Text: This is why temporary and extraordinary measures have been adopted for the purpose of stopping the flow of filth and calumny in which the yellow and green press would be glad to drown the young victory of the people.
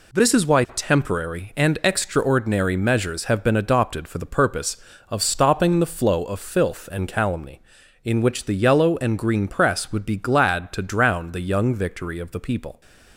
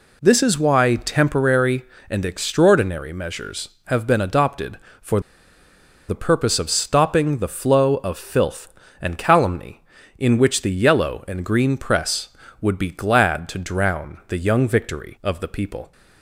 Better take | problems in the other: first | pauses between "for" and "the"; noticeable; at 5.2 s; 0.87 s long

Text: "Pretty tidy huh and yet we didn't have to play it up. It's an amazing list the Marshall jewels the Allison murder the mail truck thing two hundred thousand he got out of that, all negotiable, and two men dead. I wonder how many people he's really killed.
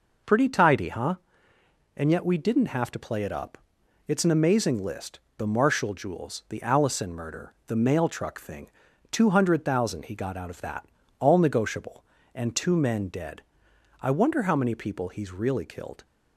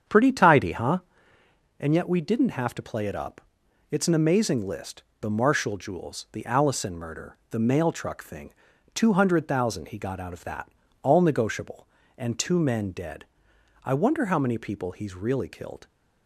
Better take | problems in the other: first | starts louder than the rest; strong; until 1.6 s; 8 dB // pauses between "list" and "the"; slight; at 5.0 s; 0.16 s long; slight in the first // pauses between "murder" and "the"; slight; at 7.3 s; 0.16 s long; slight in the first // pauses between "thing" and "two"; at 8.5 s; 0.40 s long; also in the first

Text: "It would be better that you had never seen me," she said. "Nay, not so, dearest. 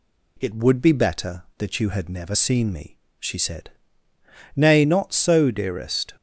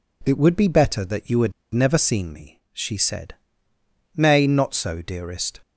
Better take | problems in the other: first | pauses between "had" and "never"; slight; at 1.5 s; 0.19 s long

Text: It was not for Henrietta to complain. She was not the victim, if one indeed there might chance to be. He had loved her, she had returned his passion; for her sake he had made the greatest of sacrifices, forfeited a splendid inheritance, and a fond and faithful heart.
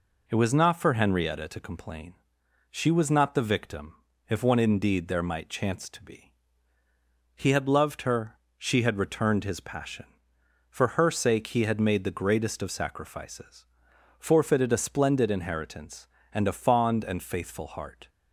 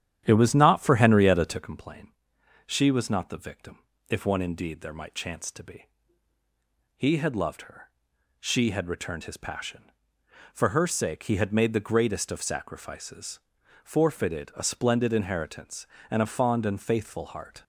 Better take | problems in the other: first | starts louder than the rest; strong; until 1.7 s; 10.5 dB

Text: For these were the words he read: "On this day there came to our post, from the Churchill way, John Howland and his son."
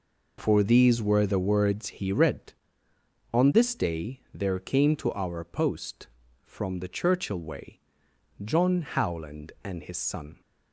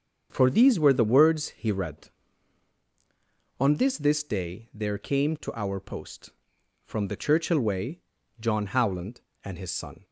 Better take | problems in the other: first | starts louder than the rest; until 1.3 s; 7 dB // says "this" twice; at 3.9 s

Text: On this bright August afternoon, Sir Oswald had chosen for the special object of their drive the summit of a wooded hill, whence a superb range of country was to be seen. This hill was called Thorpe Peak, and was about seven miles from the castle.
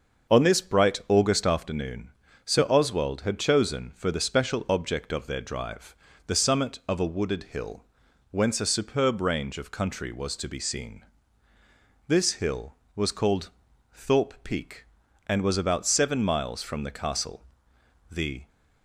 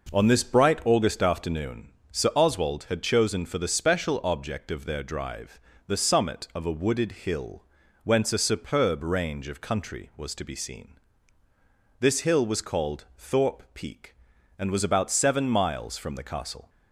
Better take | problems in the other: second | starts louder than the rest; until 1.3 s; 6.5 dB // pauses between "drive" and "the"; slight; at 5.9 s; 0.30 s long; slight in the second // pauses between "called" and "Thorpe"; noticeable; at 13.4 s; 0.46 s long // goes on to say "The"; slight; from 18.1 s on; 0.36 s long

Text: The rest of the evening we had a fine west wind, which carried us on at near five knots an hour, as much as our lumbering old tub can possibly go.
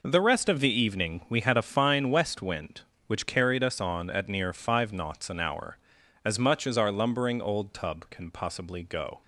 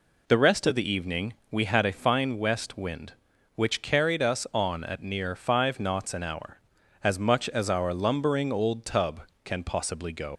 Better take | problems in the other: first | pauses between "evening" and "we"; slight; at 1.3 s; 0.18 s long // leaves "go" unfinished; at 10.3 s; 100 ms

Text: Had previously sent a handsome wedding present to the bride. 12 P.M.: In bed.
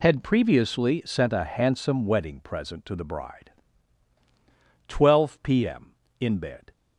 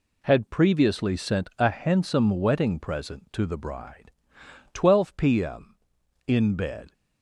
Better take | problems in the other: neither | none

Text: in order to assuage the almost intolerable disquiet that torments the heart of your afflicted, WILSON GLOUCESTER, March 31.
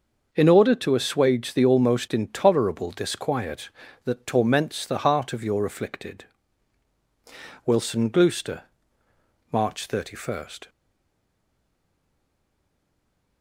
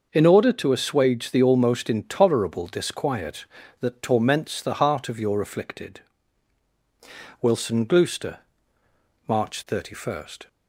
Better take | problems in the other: second | starts louder than the rest; noticeable; until 1.3 s; 6 dB // stays silent after the last word; strong; from 10.6 s on; 2.8 s long

